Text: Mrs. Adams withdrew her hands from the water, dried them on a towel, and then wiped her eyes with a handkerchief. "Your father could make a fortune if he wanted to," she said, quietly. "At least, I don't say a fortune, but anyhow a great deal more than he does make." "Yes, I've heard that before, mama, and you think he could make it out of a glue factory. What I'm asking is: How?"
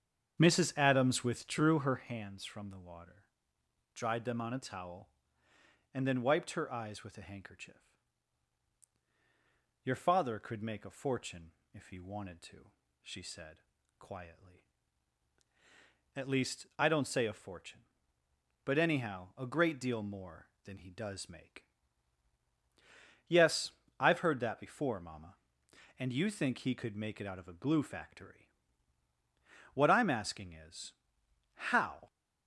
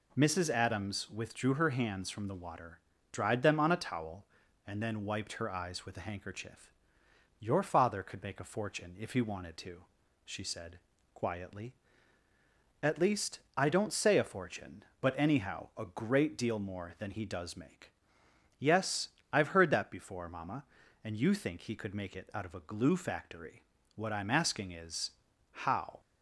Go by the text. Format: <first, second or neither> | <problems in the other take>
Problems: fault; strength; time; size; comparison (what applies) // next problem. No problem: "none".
second | starts louder than the rest; strong; until 2.0 s; 7.5 dB // pauses between "fortune" and "if"; slight; at 11.5 s; 0.20 s long